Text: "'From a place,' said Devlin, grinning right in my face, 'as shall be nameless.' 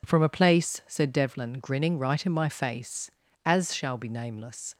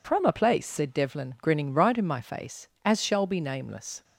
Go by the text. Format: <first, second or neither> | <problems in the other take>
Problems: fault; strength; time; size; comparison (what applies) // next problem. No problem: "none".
neither | none